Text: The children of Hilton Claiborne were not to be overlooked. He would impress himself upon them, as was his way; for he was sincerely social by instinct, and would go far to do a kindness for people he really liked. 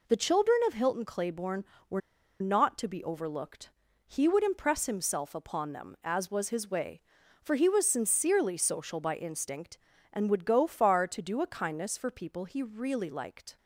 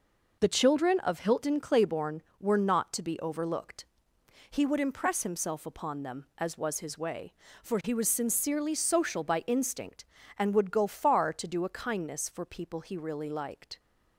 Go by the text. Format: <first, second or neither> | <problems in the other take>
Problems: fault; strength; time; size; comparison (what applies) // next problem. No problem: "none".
second | pauses between "were" and "not"; at 2.0 s; 0.40 s long